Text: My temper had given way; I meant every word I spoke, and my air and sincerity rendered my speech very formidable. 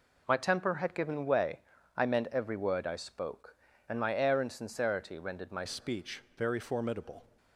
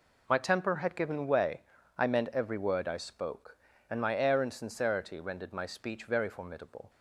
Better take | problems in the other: second | changes voice at "speech"; from 5.6 s on; 1.6 s long // pauses between "speech" and "very"; slight; at 6.2 s; 0.16 s long

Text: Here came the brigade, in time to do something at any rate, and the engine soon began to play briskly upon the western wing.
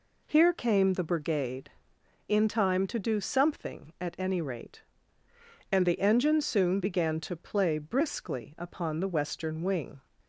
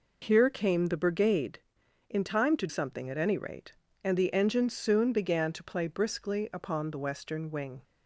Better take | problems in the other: first | skips "do"; at 2.6 s

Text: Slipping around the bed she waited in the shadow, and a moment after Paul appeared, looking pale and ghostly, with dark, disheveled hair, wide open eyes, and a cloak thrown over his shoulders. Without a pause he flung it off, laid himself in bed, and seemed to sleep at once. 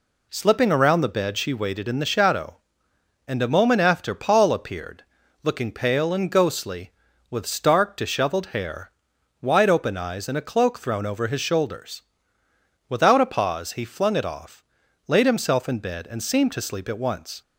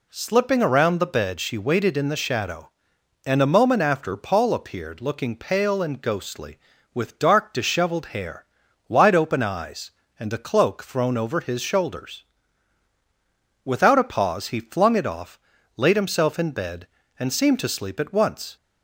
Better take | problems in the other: second | says "stark" for "dark"; at 7.4 s

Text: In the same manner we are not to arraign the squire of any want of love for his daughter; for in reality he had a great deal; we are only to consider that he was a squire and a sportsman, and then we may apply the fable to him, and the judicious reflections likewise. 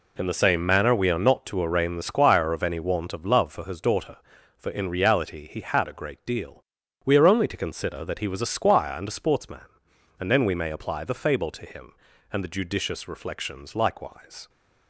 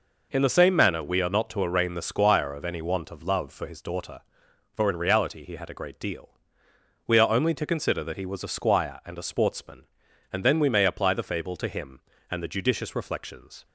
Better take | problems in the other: first | stops before "likewise"; at 13.6 s

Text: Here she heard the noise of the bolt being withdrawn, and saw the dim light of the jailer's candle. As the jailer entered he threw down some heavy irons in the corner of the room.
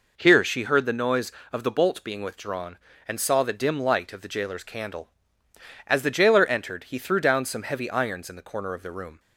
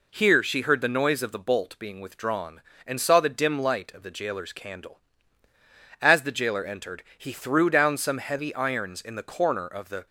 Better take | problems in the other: first | stops before "room"; at 10.0 s

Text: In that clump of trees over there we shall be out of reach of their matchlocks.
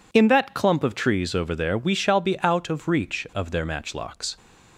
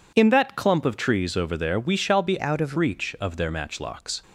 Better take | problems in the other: first | changes voice from "out" to "of"; from 2.4 to 2.7 s; 0.3 s long

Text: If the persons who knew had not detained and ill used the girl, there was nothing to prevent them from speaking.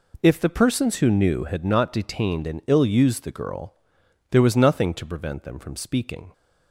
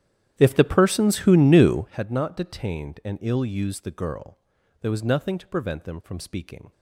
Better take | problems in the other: first | starts louder than the rest; strong; until 2.0 s; 11 dB

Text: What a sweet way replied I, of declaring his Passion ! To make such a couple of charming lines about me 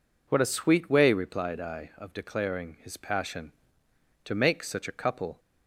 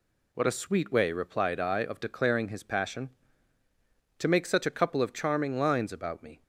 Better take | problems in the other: second | stops before "of charming lines about me"; at 5.3 s

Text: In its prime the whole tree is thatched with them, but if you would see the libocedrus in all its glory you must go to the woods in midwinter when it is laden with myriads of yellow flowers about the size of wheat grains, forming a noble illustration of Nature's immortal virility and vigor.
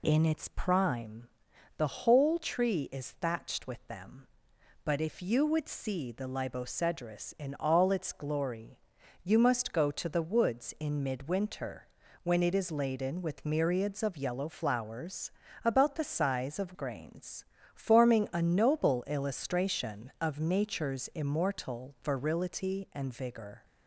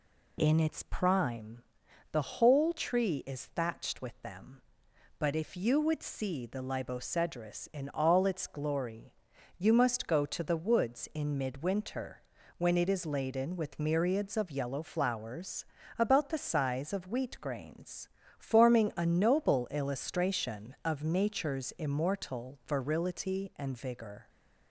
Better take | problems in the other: second | pauses between "prime" and "the"; noticeable; at 1.2 s; 0.50 s long; noticeable in the second // pauses between "glory" and "you"; noticeable; at 8.7 s; 0.46 s long; noticeable in the second // pauses between "midwinter" and "when"; slight; at 11.8 s; 0.36 s long; slight in the second // pauses between "flowers" and "about"; slight; at 15.3 s; 0.34 s long; slight in the second // skips "wheat"; at 16.7 s

